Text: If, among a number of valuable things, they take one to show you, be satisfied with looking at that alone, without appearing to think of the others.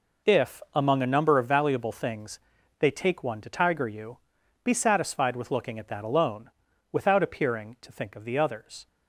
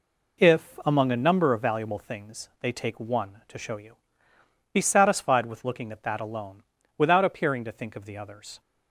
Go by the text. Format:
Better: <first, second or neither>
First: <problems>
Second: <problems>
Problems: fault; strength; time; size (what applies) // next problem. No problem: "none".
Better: second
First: says "tiger" for "show"; at 3.4 s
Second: none